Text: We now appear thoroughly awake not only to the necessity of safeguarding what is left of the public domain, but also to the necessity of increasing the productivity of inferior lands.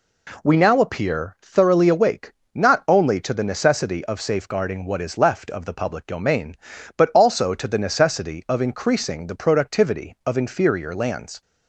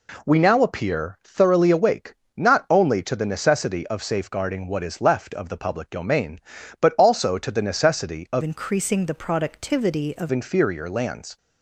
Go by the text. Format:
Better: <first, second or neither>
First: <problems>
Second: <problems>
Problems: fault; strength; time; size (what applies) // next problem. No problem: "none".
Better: first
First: pauses between "awake" and "not"; slight; at 2.3 s; 0.22 s long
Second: pauses between "awake" and "not"; slight; at 2.1 s; 0.22 s long // changes voice from "increasing" to "of"; from 8.4 to 10.3 s; 1.9 s long